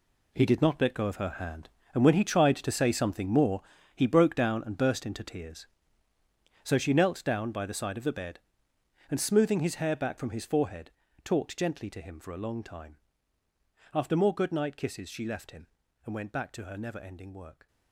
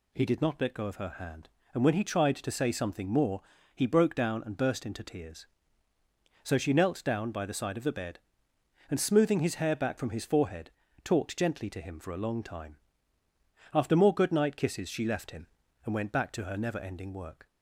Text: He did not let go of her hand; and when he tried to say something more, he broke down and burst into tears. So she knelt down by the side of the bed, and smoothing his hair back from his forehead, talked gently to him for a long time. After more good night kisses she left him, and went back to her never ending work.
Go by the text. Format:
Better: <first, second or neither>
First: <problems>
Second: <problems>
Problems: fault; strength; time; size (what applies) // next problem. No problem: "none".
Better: second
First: gets quieter; strong; throughout; 11.5 dB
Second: none